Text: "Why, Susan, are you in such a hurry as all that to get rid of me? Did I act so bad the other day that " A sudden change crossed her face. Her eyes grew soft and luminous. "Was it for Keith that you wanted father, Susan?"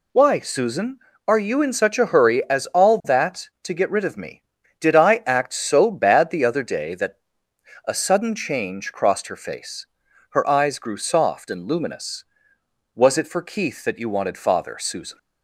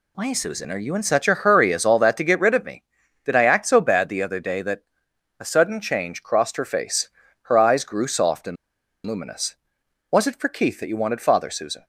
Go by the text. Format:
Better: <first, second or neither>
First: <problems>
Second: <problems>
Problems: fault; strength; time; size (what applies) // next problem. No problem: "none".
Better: first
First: none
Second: pauses between "and" and "luminous"; noticeable; at 8.5 s; 0.50 s long